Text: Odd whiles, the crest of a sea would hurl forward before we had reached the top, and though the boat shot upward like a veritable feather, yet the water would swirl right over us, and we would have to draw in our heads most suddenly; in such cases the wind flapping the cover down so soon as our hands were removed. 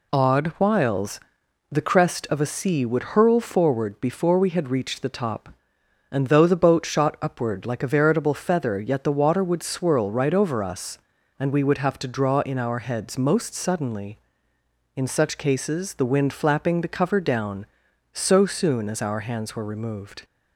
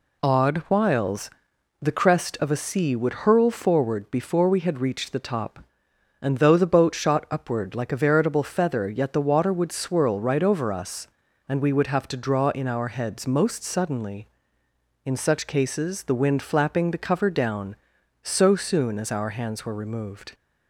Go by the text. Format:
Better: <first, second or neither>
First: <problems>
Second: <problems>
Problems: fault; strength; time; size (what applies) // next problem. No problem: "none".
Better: neither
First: none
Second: none